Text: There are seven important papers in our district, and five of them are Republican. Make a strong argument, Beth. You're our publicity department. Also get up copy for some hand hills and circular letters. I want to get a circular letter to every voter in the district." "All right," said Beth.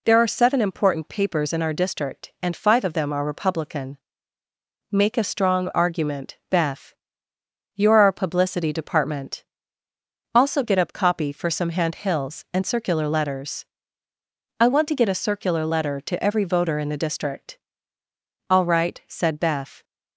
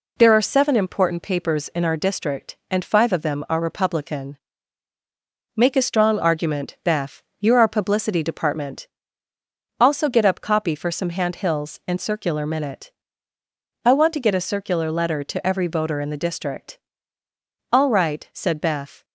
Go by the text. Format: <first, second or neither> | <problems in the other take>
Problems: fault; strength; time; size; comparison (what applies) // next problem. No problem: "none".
first | says "minute" for "letters"; at 12.4 s